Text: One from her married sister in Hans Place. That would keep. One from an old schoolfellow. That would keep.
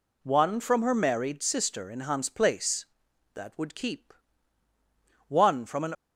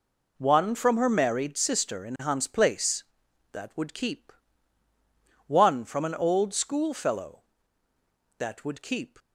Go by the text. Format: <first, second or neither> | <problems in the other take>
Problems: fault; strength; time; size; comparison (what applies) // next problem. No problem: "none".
second | stops before "old schoolfellow That would keep"; at 5.9 s